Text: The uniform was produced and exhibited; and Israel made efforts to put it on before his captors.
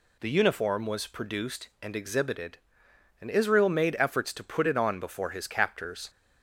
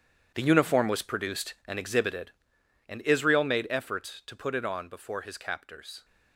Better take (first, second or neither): first